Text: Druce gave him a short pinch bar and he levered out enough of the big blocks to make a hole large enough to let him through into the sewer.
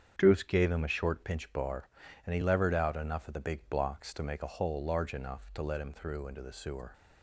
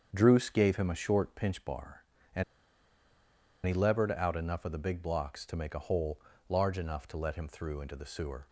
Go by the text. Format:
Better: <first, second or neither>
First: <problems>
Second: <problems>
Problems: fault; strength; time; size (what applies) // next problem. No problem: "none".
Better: first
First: starts louder than the rest; strong; until 1.1 s; 8 dB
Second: starts louder than the rest; strong; until 1.1 s; 7 dB // pauses between "and" and "he"; at 2.4 s; 1.2 s long // pauses between "hole" and "large"; slight; at 6.1 s; 0.30 s long